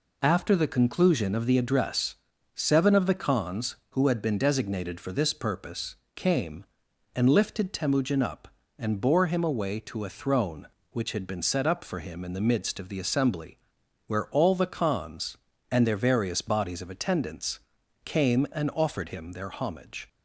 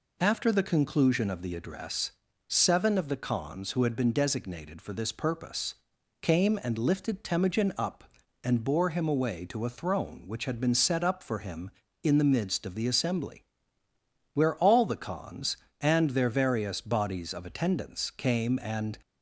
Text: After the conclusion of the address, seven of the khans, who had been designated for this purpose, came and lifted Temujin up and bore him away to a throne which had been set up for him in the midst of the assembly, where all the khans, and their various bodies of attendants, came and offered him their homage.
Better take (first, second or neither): first